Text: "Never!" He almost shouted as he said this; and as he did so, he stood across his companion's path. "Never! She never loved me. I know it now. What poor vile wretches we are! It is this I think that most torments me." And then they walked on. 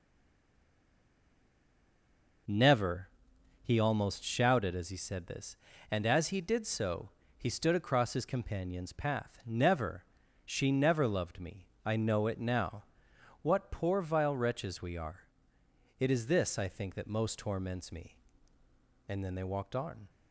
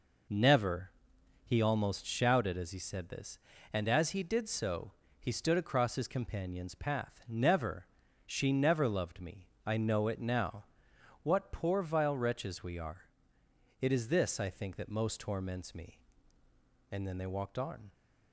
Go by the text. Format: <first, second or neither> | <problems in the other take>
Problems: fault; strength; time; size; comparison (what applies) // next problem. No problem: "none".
second | stays silent before the first word; until 2.4 s; 2.4 s long